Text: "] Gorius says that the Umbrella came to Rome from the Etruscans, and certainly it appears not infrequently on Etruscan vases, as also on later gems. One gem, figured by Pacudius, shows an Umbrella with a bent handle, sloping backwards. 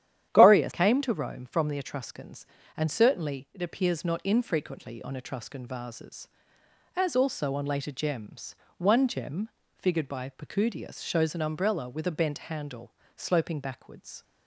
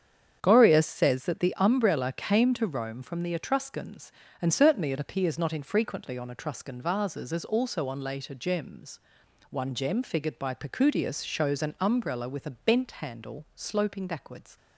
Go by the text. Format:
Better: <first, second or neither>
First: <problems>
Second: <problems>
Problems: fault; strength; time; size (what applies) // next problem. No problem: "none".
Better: second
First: starts louder than the rest; strong; until 1.3 s; 10.5 dB // skips "says that the Umbrella"; at 0.7 s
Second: starts louder than the rest; strong; until 1.4 s; 7.5 dB